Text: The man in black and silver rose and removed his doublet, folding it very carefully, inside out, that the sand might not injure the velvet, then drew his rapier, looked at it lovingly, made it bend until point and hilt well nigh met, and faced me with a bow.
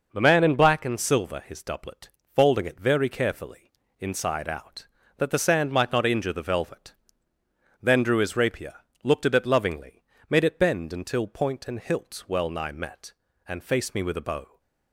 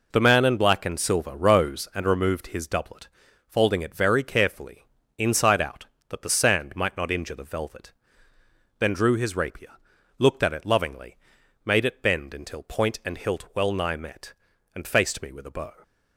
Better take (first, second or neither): second